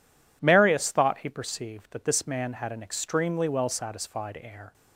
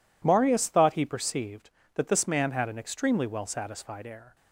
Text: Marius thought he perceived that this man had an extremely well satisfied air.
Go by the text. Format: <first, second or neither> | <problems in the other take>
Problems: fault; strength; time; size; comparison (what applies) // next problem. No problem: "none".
neither | none